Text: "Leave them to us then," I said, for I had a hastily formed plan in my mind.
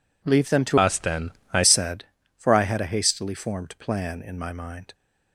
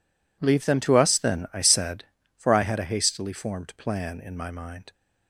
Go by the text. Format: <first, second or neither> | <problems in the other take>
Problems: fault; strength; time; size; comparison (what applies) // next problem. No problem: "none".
second | changes voice from "us" to "I"; from 0.7 to 1.6 s; 0.9 s long